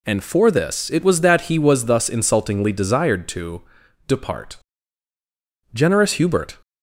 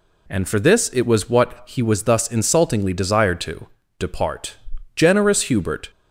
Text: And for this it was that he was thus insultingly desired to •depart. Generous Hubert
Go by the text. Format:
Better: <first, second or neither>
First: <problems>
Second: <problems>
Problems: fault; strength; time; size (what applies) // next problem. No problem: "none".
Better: first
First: none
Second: says "what" for "that"; at 1.2 s